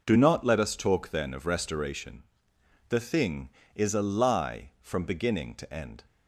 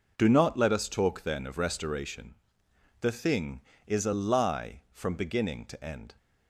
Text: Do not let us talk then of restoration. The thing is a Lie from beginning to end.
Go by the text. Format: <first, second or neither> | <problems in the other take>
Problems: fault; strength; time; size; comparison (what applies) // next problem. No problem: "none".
neither | none